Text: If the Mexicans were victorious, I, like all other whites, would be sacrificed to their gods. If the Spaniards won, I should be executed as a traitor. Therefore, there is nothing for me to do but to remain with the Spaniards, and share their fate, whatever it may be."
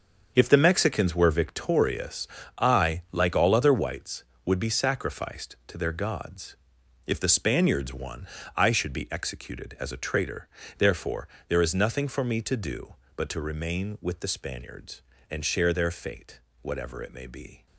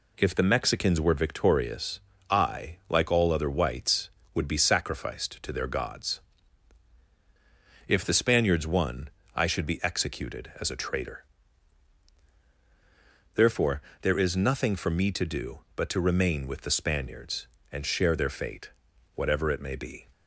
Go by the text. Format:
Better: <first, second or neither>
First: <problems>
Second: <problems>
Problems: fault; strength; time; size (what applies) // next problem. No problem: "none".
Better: second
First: gets quieter; strong; throughout; 11 dB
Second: none